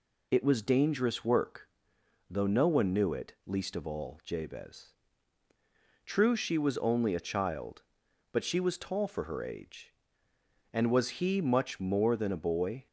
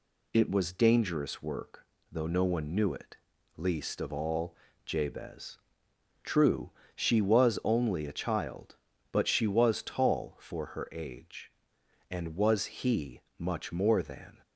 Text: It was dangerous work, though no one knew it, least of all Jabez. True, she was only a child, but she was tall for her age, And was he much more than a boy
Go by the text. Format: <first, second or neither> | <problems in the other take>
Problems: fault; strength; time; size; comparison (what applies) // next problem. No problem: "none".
first | pauses between "all" and "Jabez"; slight; at 4.5 s; 0.30 s long // pauses between "he" and "much"; slight; at 13.2 s; 0.18 s long // stops before "a boy"; at 14.4 s